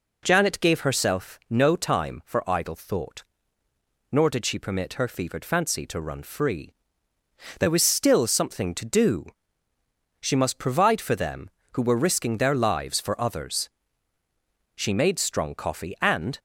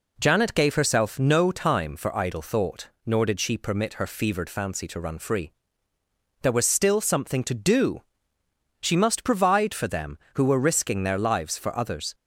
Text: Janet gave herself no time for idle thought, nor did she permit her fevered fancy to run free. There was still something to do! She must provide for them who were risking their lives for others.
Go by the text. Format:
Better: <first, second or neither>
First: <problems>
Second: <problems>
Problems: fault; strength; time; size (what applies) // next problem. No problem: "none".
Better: second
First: goes on to say "She made strong coffee and"; from 14.7 s on; 1.6 s long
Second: none